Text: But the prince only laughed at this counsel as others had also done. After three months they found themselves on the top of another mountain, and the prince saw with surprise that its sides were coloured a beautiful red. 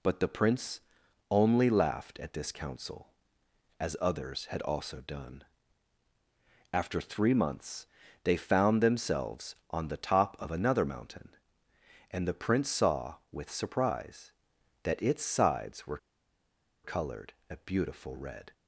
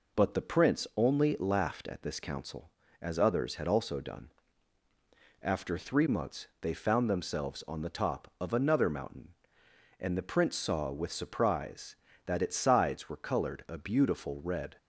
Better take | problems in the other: second | pauses between "prince" and "only"; noticeable; at 0.8 s; 0.50 s long // pauses between "months" and "they"; at 7.8 s; 0.38 s long // pauses between "were" and "coloured"; noticeable; at 15.9 s; 0.87 s long // pauses between "coloured" and "a"; slight; at 17.3 s; 0.18 s long

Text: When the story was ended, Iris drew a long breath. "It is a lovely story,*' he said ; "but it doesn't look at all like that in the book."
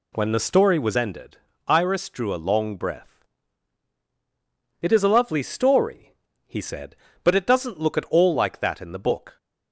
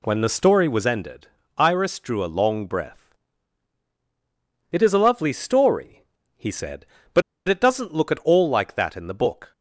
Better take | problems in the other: first | pauses between "but" and "it"; slight; at 7.2 s; 0.26 s long

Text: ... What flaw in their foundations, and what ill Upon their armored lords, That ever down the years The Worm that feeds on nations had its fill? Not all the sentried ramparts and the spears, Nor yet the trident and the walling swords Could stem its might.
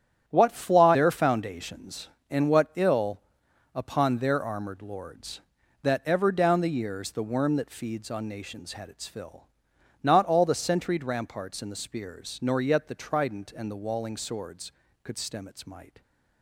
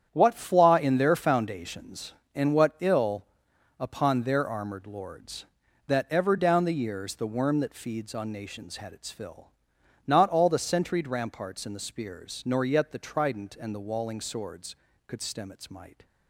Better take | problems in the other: second | starts louder than the rest; strong; until 1.2 s; 10 dB; strong in the second // skips "in"; at 0.9 s // pauses between "ill" and "Upon"; noticeable; at 3.2 s; 0.52 s long; noticeable in the second

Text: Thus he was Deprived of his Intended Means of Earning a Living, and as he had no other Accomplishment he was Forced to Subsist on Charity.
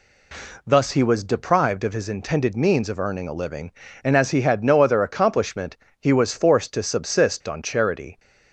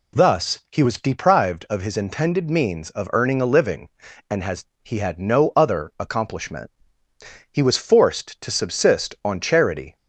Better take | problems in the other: first | says "has" for "as"; at 4.4 s // pauses between "Accomplishment" and "he"; noticeable; at 6.7 s; 0.80 s long; slight in the first

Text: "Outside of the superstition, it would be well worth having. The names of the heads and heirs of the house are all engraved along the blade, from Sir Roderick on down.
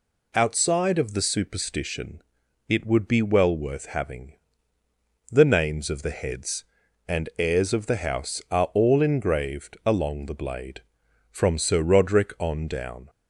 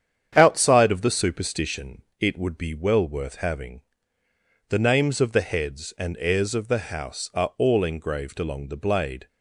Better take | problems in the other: first | starts louder than the rest; strong; until 1.3 s; 9 dB // stops before "from Sir Roderick on down"; at 9.2 s

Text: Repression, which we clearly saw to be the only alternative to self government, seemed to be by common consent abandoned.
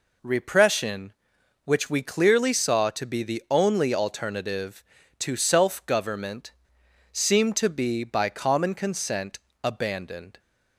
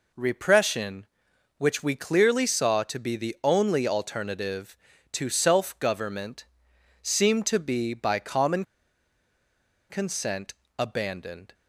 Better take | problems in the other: first | pauses between "common" and "consent"; strong; at 8.6 s; 1.2 s long // pauses between "consent" and "abandoned"; slight; at 10.5 s; 0.26 s long; slight in the first

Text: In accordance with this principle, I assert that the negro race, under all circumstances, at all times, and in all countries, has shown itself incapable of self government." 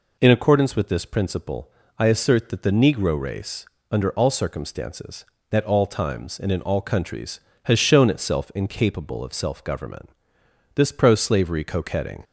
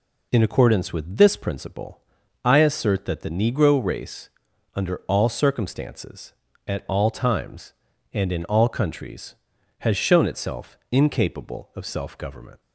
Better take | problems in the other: second | goes on to say "This pro slavery coquetting"; from 10.7 s on; 1.5 s long

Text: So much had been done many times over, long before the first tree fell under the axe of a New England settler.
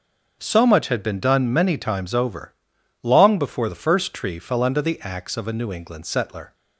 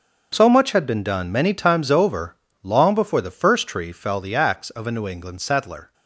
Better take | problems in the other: first | starts louder than the rest; until 1.3 s; 6.5 dB; also in the first // skips "under"; at 4.1 s

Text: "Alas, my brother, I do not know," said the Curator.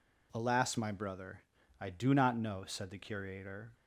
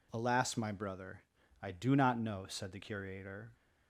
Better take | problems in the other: neither | none

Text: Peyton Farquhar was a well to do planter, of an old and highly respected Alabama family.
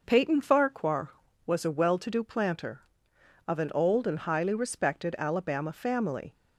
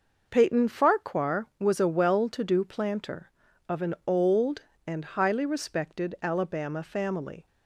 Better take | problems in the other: neither | none

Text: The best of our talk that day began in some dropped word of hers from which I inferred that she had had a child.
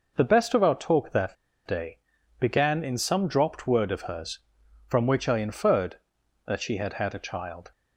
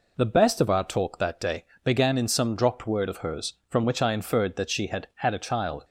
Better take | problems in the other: second | pauses between "that" and "day"; slight; at 1.3 s; 0.32 s long // pauses between "day" and "began"; at 1.9 s; 0.38 s long; slight in the second

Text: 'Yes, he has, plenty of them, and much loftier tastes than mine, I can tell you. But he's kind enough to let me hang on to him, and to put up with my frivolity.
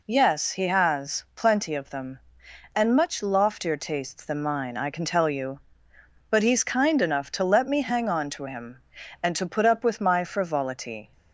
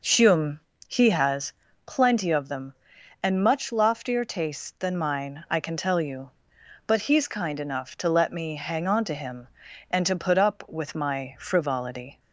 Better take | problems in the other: first | says "Hume" for "Yes"; at 0.0 s

